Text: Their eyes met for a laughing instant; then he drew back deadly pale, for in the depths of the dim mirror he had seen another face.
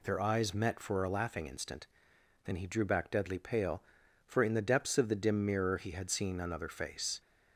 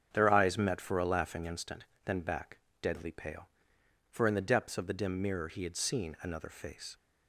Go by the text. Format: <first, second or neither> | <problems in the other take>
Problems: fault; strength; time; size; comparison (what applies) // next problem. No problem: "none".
first | starts louder than the rest; strong; until 1.1 s; 7.5 dB // skips "he drew"; at 2.1 s // pauses between "back" and "deadly"; slight; at 2.5 s; 0.24 s long